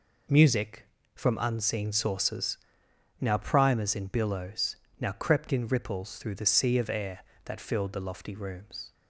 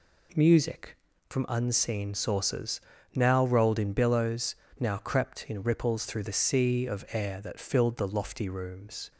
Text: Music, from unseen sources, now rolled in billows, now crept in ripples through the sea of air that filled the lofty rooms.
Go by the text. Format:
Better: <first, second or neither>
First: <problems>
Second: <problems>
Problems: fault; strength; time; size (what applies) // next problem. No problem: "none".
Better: second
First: says "primers" for "rolled"; at 3.3 s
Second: none